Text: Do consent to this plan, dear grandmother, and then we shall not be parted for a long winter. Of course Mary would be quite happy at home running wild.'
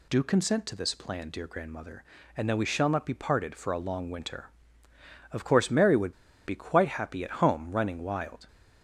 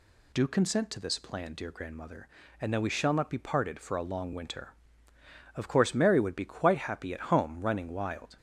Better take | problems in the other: second | pauses between "would" and "be"; slight; at 6.1 s; 0.34 s long

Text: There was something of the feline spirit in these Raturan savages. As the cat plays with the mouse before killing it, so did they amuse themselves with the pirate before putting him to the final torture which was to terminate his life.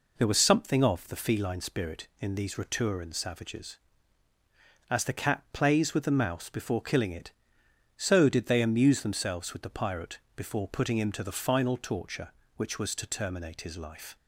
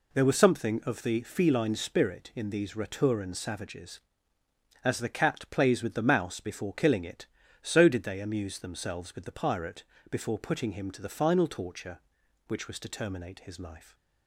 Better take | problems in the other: neither | pauses between "pirate" and "before"; slight; the same in both

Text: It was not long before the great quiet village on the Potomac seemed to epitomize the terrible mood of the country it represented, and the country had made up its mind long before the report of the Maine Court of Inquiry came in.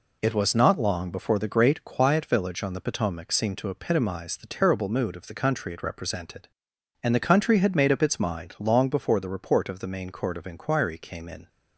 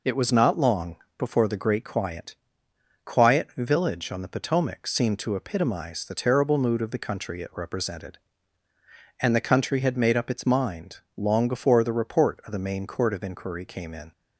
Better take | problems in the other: first | pauses between "long" and "before"; slight; at 0.9 s; 0.22 s long // says "quiet" twice; at 3.0 s // pauses between "mind" and "long"; slight; at 10.9 s; 0.18 s long

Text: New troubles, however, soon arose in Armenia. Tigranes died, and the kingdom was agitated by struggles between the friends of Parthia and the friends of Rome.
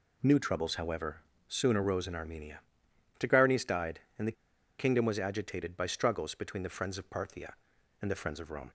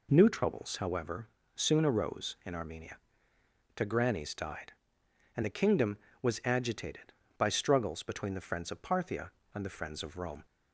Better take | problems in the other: second | pauses between "the" and "kingdom"; at 4.3 s; 0.45 s long

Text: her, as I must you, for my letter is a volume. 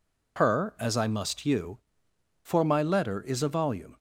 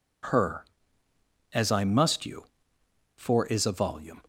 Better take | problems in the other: first | skips "my letter"; at 3.4 s

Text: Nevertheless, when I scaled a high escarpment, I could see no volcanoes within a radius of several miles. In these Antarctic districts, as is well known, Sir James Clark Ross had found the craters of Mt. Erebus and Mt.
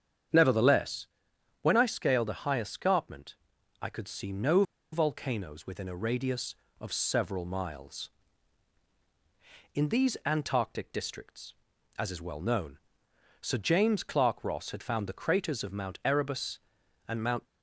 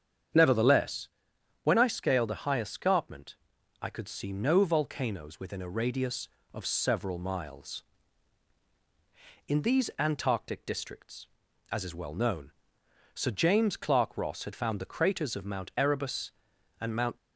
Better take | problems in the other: second | starts louder than the rest; strong; until 1.8 s; 8 dB; strong in the second // pauses between "no" and "volcanoes"; slight; at 4.6 s; 0.29 s long

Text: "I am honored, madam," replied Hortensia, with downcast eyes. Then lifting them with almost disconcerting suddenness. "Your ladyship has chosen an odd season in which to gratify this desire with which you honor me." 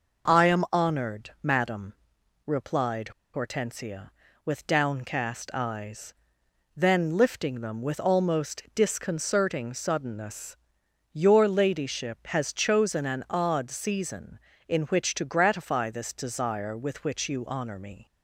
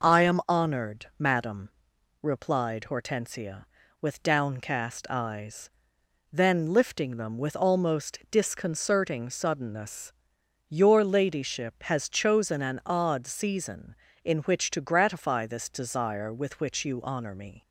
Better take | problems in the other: second | pauses between "replied" and "Hortensia"; slight; at 3.1 s; 0.23 s long

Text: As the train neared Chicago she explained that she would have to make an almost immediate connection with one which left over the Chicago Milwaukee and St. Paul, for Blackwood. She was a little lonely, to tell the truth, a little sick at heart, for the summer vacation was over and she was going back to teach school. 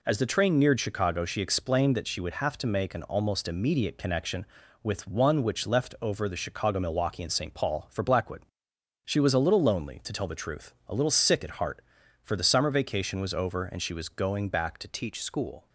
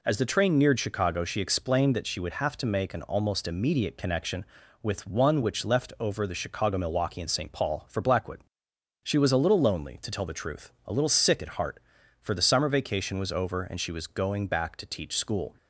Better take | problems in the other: second | changes voice at "teach"; from 14.8 s on; 0.8 s long

